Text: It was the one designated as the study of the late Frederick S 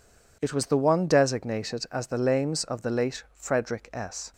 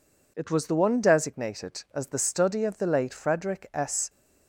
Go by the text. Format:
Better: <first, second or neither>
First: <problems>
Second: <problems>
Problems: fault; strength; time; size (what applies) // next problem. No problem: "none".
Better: second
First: says "lames" for "study"; at 2.1 s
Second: none